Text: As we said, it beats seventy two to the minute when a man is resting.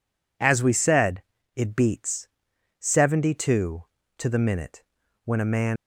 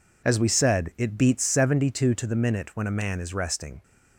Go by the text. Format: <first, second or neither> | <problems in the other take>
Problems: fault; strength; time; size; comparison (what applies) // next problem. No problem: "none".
second | pauses between "beats" and "seventy"; noticeable; at 2.2 s; 0.52 s long // pauses between "minute" and "when"; at 4.8 s; 0.42 s long // stops before "is resting"; at 5.7 s